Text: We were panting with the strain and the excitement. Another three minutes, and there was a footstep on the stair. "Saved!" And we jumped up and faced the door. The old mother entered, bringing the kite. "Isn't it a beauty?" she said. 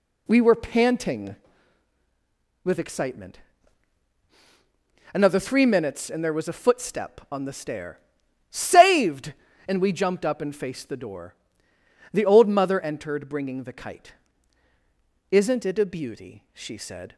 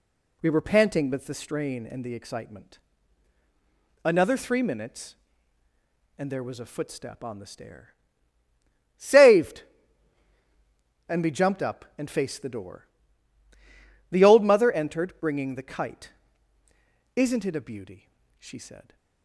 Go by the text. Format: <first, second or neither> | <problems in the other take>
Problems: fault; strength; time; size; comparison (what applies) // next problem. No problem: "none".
second | skips "the strain and the"; at 2.7 s